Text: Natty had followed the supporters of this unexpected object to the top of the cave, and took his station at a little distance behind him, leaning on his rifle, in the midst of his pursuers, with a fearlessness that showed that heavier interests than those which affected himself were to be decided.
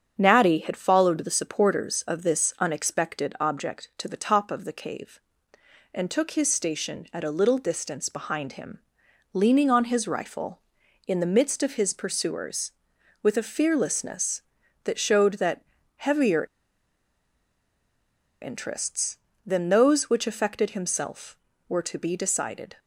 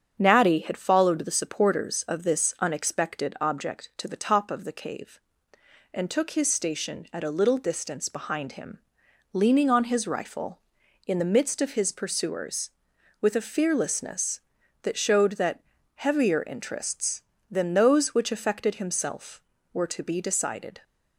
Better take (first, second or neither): second